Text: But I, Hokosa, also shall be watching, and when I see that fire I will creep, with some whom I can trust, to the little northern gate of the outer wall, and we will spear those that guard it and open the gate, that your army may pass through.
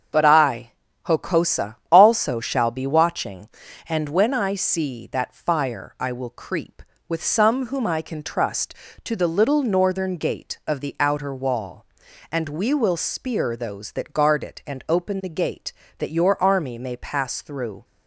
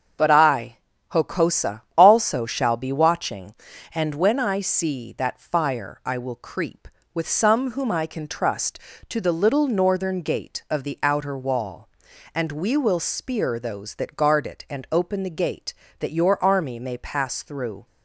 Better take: neither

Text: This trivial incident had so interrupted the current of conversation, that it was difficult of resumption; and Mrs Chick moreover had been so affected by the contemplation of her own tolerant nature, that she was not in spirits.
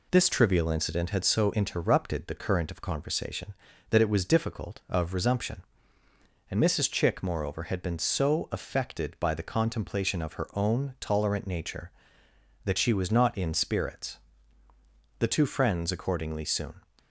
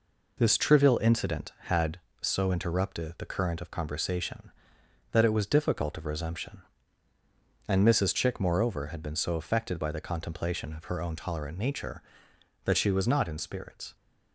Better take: second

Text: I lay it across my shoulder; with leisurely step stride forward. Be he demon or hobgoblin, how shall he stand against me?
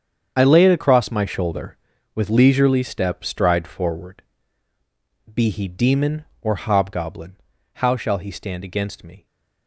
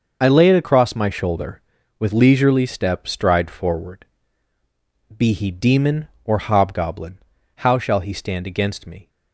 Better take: second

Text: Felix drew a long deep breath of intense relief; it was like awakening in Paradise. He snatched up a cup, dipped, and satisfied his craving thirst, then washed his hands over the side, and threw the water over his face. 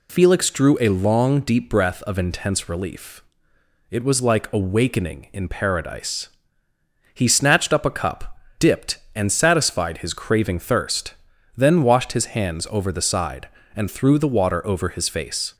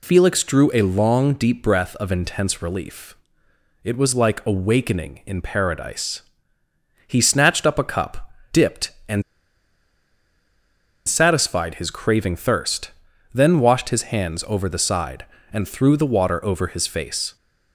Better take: first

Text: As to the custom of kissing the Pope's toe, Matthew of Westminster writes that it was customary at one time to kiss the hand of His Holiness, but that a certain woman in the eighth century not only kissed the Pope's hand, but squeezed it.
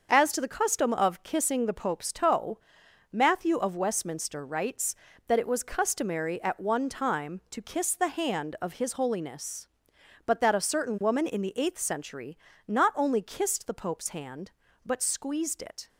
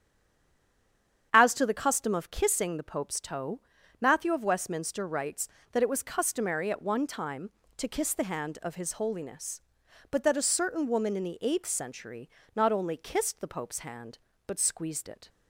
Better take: first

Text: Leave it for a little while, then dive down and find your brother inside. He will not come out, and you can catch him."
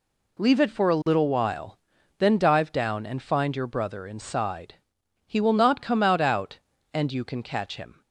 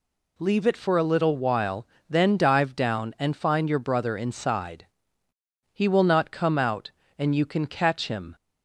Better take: second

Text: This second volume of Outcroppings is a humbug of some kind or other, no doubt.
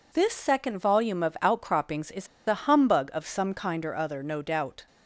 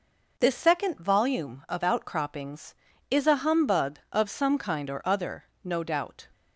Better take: second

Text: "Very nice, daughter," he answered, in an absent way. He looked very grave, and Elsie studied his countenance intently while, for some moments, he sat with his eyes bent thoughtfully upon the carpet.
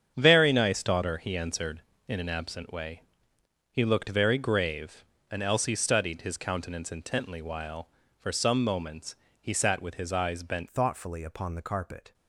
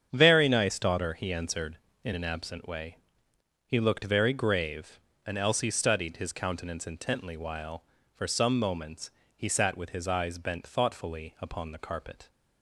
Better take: second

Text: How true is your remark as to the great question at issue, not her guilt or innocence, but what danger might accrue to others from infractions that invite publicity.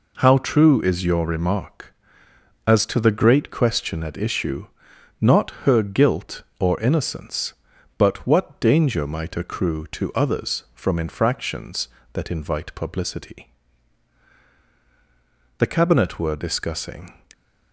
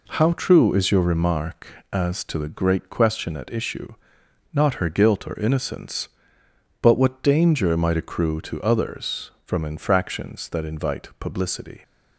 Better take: second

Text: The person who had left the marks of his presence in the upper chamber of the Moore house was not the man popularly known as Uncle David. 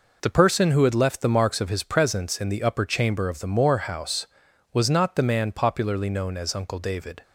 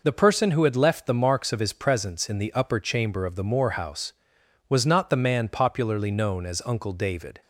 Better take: neither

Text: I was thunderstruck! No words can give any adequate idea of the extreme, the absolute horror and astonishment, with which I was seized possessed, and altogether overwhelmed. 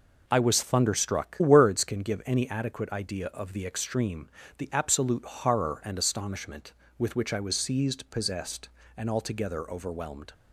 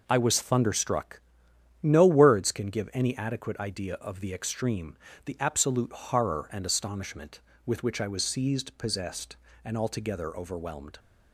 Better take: second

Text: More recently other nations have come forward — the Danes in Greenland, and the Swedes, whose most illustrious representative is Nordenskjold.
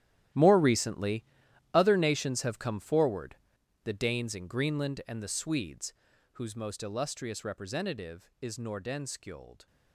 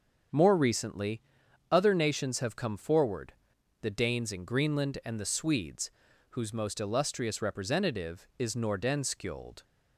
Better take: second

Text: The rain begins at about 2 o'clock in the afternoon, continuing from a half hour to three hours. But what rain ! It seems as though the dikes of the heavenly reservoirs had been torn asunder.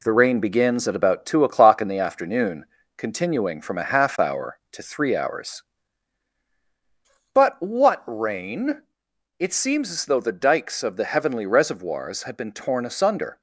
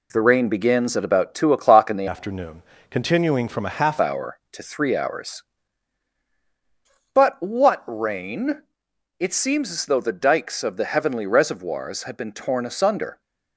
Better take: first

